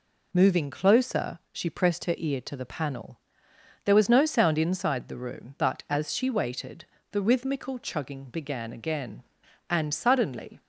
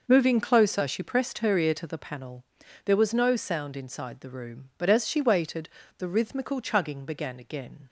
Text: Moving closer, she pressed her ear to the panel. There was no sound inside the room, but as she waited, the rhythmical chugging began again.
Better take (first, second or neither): second